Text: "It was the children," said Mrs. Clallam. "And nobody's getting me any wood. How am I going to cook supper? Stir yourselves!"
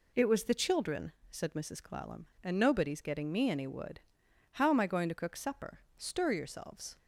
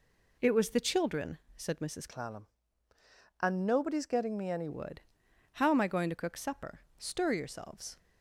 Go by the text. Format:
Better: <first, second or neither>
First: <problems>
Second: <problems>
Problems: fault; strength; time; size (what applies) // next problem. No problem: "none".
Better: first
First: none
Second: changes voice from "Clallam" to "any"; from 2.0 to 4.6 s; 2.6 s long